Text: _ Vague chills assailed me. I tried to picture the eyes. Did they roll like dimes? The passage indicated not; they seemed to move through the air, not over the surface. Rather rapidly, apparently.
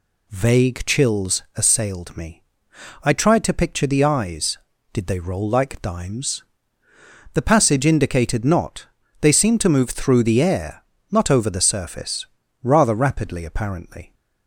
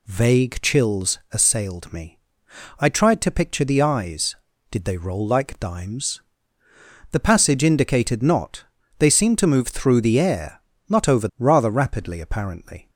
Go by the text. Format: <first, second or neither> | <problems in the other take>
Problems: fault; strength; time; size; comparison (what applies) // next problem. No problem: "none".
first | skips "the surface"; at 11.3 s